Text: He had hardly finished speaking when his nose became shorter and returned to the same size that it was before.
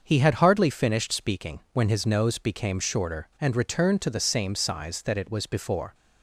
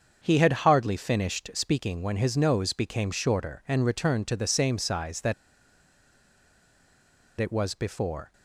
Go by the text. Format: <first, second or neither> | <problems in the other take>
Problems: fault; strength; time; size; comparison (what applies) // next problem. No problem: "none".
first | starts louder than the rest; until 1.2 s; 6.5 dB; also in the first // pauses between "that" and "it"; strong; at 5.3 s; 2.0 s long